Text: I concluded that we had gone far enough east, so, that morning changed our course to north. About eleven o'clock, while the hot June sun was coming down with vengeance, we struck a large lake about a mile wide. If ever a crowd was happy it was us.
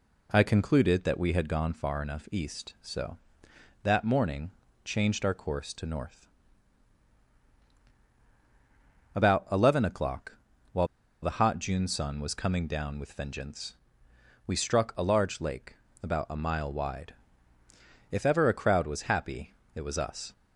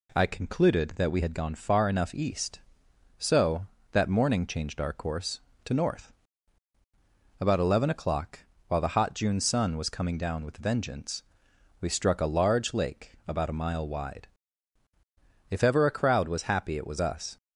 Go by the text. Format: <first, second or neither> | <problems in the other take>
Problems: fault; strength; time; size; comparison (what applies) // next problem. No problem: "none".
second | pauses between "morning" and "changed"; slight; at 4.5 s; 0.34 s long // pauses between "while" and "the"; slight; at 10.8 s; 0.35 s long // pauses between "lake" and "about"; slight; at 15.7 s; 0.26 s long // pauses between "happy" and "it"; slight; at 19.5 s; 0.24 s long